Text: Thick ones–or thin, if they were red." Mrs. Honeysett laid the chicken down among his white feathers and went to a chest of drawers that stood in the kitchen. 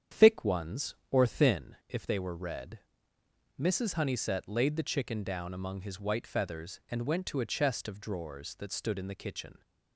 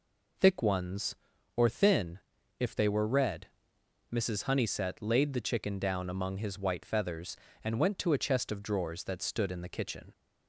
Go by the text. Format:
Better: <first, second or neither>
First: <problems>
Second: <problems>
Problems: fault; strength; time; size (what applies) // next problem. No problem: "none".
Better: second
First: starts louder than the rest; strong; until 1.6 s; 8.5 dB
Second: none